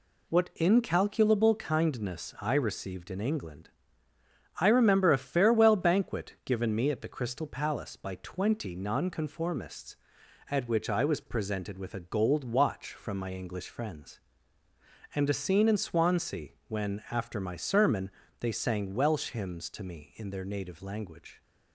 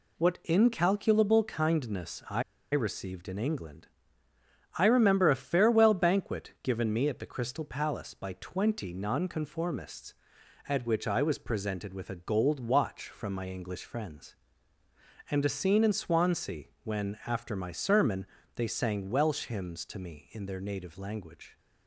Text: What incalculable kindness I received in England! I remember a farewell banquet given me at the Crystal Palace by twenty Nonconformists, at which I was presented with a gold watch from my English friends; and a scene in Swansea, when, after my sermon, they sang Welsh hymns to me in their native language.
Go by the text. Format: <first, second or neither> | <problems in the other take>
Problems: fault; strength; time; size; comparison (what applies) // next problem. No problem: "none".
first | pauses between "I" and "received"; slight; at 2.4 s; 0.30 s long